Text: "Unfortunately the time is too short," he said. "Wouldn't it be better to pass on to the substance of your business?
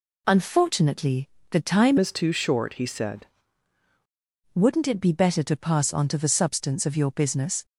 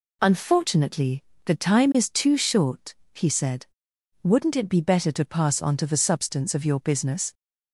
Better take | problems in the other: second | pauses between "Unfortunately" and "the"; slight; at 1.2 s; 0.22 s long; slight in the second // changes voice from "is" to "said"; from 1.9 to 3.2 s; 1.3 s long

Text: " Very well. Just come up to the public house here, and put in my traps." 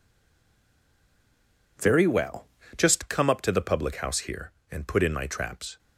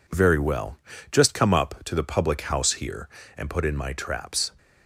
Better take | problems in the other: second | stays silent before the first word; noticeable; until 1.7 s; 1.7 s long

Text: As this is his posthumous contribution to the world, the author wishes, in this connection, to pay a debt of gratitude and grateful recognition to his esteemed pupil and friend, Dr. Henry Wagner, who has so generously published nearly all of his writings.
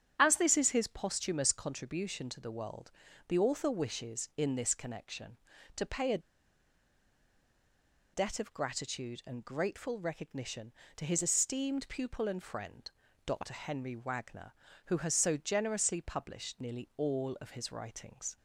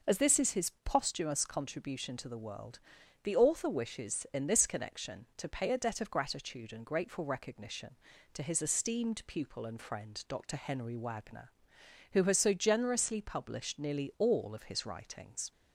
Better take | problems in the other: second | starts louder than the rest; strong; until 1.1 s; 9 dB // pauses between "a" and "debt"; strong; at 6.1 s; 1.9 s long

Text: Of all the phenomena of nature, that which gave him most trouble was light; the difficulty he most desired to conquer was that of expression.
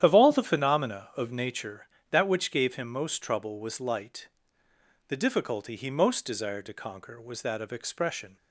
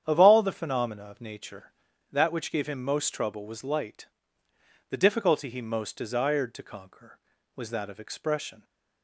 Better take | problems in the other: second | loses the start of "Of"; at 0.0 s; 35 ms // starts louder than the rest; strong; until 1.0 s; 10.5 dB; strong in the second

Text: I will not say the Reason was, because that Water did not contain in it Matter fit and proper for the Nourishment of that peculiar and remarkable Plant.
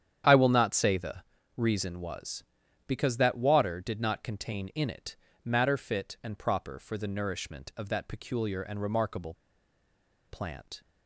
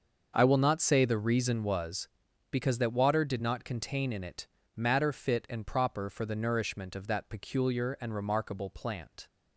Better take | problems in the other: second | starts louder than the rest; strong; until 1.6 s; 9 dB; also in the second // pauses between "the" and "Reason"; slight; at 1.2 s; 0.32 s long // pauses between "it" and "Matter"; slight; at 5.1 s; 0.32 s long; slight in the second // pauses between "remarkable" and "Plant"; noticeable; at 9.3 s; 0.93 s long

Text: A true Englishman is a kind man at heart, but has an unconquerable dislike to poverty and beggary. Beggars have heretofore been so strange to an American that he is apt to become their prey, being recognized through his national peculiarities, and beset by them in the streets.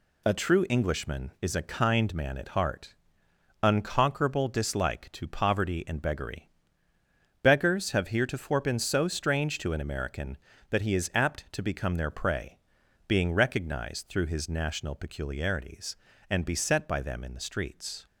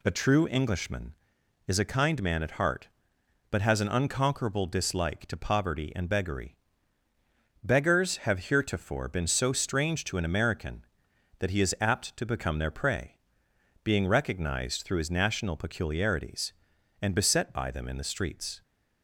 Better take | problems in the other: second | skips "but has an"; at 3.2 s

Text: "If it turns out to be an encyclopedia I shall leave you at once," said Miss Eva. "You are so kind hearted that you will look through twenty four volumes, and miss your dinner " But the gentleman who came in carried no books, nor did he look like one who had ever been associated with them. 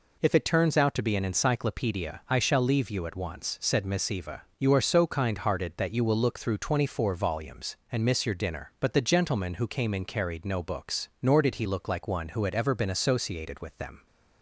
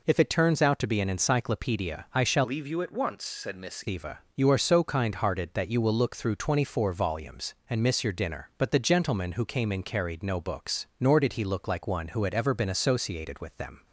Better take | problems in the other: first | changes voice from "leave" to "Miss"; from 2.4 to 3.8 s; 1.4 s long

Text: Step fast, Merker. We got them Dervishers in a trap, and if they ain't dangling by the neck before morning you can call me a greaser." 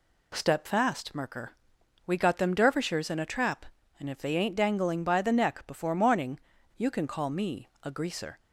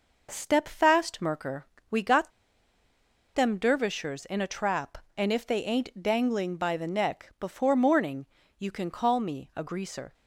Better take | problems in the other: first | pauses between "got" and "them"; at 2.2 s; 1.0 s long // pauses between "morning" and "you"; slight; at 8.2 s; 0.32 s long; also in the first

